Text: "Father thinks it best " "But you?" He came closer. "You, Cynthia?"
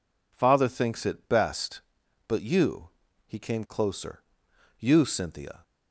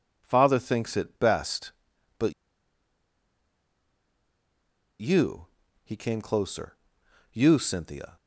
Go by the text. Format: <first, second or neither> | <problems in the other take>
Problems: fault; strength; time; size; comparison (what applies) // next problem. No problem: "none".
first | pauses between "But" and "you"; strong; at 2.3 s; 2.6 s long